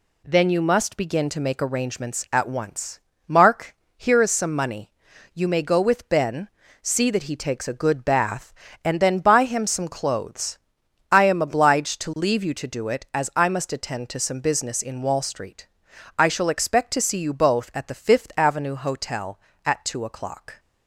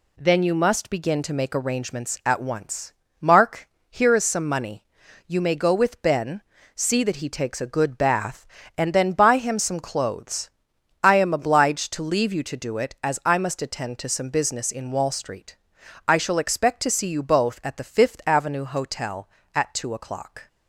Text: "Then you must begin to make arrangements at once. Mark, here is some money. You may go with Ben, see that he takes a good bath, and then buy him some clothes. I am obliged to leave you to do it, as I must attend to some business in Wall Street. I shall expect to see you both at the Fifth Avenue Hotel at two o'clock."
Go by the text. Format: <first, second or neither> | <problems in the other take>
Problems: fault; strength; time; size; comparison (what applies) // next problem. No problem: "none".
neither | none